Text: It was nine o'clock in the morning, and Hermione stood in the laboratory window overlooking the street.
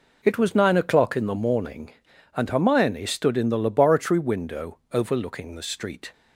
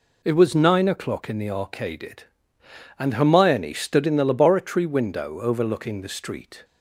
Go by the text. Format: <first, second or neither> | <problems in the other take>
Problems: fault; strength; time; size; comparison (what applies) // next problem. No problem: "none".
first | says "arcaded" for "morning"; at 1.5 s